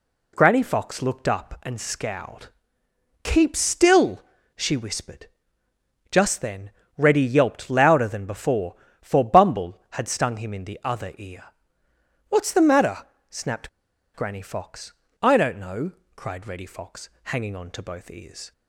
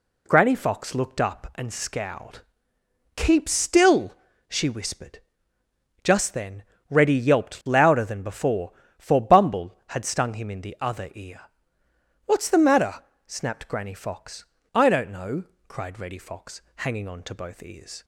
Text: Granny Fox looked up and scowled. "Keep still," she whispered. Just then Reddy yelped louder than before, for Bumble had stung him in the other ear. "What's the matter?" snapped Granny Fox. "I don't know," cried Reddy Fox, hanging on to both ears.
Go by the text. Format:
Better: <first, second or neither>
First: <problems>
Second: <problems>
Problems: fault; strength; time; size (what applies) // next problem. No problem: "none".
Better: second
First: pauses between "then" and "Reddy"; slight; at 6.7 s; 0.26 s long // pauses between "snapped" and "Granny"; at 13.6 s; 0.44 s long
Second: pauses between "then" and "Reddy"; slight; at 6.6 s; 0.26 s long